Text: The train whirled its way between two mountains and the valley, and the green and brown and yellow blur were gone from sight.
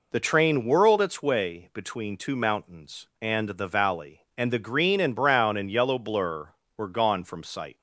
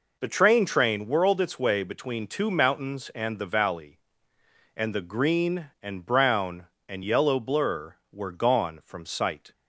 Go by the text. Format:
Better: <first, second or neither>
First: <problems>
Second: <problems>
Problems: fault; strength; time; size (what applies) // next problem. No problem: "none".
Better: first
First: none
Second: says "train" twice; at 0.6 s